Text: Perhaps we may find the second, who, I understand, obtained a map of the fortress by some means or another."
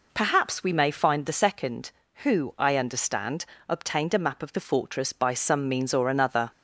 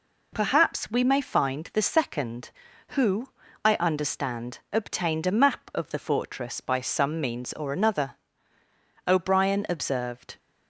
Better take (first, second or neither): first